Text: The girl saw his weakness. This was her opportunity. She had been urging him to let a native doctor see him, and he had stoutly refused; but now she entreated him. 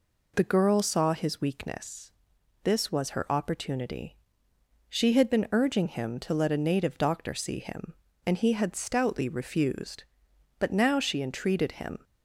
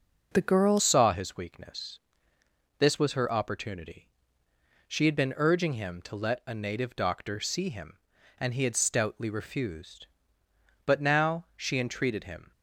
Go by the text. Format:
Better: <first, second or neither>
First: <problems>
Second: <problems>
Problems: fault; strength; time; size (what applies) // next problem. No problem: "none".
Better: first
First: none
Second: changes voice at "saw"; from 0.7 s on; 11.8 s long